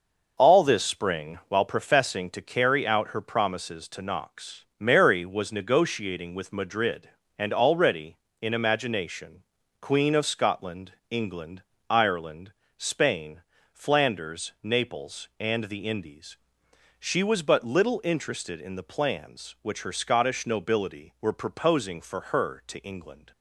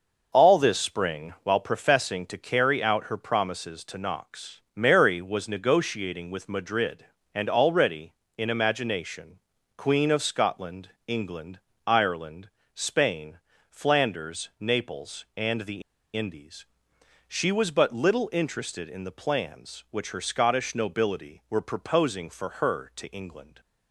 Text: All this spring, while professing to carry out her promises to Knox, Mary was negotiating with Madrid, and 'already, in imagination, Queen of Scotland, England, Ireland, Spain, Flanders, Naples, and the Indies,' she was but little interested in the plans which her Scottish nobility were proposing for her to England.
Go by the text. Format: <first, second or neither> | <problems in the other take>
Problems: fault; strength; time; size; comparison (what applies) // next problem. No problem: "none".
first | pauses between "the" and "Indies"; slight; at 15.8 s; 0.33 s long